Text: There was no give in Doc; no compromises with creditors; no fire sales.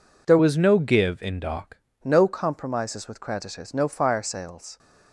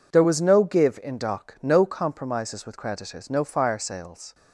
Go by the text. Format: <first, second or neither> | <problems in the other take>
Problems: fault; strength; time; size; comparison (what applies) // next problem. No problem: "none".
second | changes voice from "was" to "Doc"; from 0.3 to 1.7 s; 1.4 s long